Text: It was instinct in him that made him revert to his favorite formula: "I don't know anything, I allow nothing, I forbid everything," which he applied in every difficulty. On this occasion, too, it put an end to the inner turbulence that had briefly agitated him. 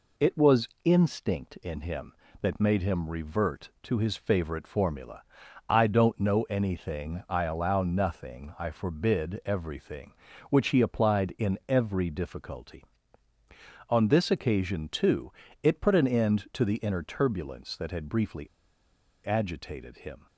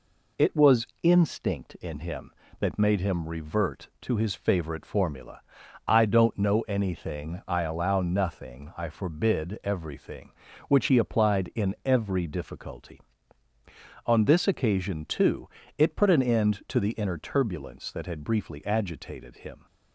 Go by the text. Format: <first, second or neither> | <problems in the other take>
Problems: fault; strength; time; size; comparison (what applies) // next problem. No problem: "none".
second | pauses between "briefly" and "agitated"; noticeable; at 18.4 s; 0.78 s long